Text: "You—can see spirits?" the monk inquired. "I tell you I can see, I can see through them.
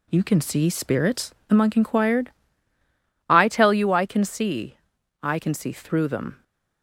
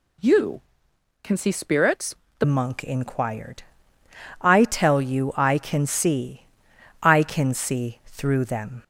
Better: first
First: none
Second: changes voice at "monk"; from 2.4 s on; 6.4 s long

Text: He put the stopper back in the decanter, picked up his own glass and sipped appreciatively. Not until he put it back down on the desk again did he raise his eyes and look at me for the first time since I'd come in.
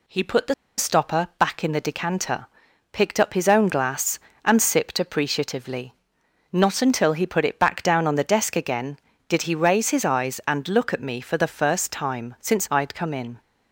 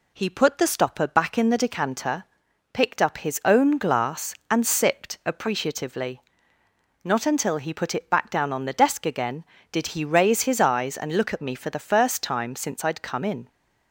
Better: second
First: pauses between "the" and "stopper"; slight; at 0.5 s; 0.23 s long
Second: none

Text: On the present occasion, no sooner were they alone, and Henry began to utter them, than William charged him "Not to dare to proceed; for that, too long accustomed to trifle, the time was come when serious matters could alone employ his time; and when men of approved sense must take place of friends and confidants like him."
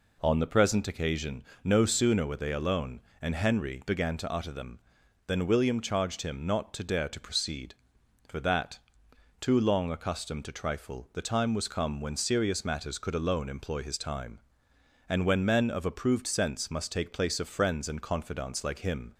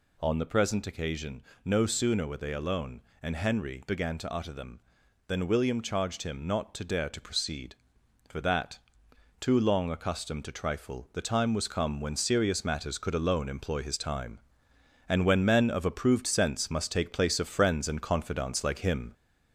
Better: first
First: none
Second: gets louder; slight; throughout; 2.5 dB

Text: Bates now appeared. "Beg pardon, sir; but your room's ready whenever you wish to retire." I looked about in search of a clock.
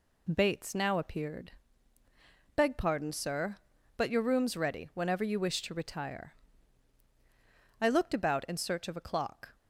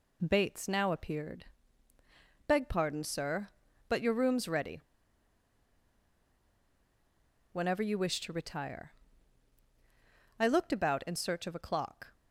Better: first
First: none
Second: pauses between "ready" and "whenever"; strong; at 4.7 s; 2.7 s long

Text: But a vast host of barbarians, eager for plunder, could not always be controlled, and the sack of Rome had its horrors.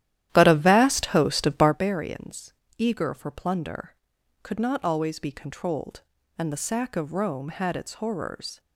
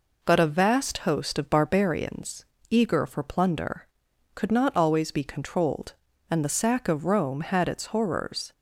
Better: second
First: starts louder than the rest; strong; until 1.8 s; 12.5 dB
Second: none

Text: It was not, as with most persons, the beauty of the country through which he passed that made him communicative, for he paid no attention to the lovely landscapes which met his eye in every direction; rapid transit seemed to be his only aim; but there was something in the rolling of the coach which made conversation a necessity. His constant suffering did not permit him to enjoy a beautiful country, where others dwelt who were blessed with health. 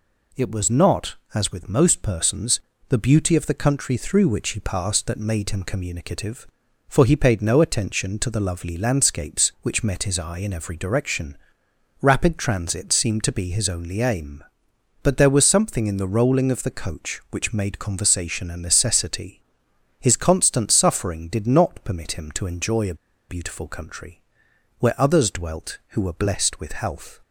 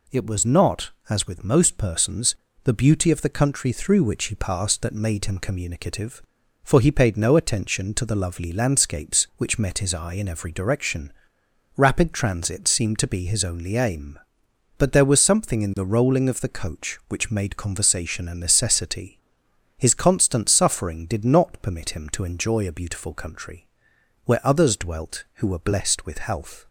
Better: second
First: pauses between "a" and "beautiful"; slight; at 22.9 s; 0.34 s long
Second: none

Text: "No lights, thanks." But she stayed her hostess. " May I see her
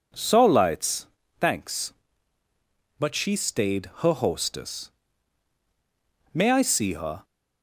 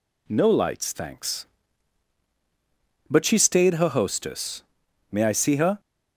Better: second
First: says "So" for "No"; at 0.1 s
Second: none

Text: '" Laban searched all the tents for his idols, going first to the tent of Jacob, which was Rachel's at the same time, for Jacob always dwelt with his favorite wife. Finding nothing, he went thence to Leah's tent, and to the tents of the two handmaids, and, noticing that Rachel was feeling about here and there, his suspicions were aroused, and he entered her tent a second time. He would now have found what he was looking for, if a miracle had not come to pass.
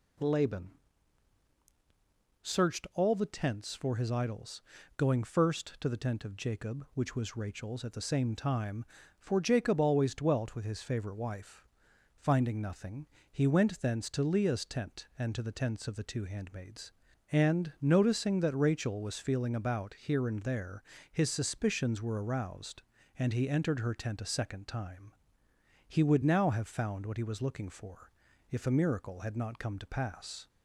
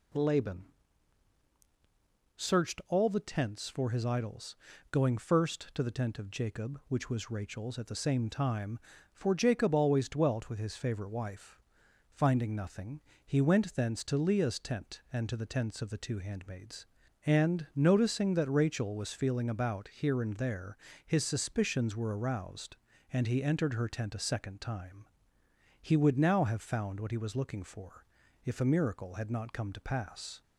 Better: neither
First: pauses between "Laban" and "searched"; strong; at 0.7 s; 1.7 s long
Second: pauses between "Laban" and "searched"; strong; at 0.6 s; 1.7 s long

